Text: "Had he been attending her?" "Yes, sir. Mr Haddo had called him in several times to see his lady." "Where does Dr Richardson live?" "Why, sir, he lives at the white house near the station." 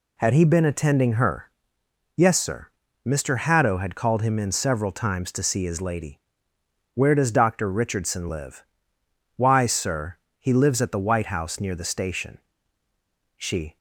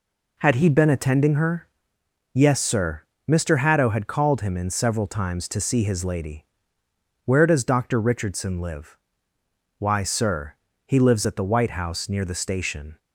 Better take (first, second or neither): second